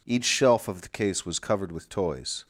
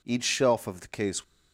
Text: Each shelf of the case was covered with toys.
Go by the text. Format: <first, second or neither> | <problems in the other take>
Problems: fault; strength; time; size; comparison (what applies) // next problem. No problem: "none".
first | stops before "was covered with toys"; at 1.2 s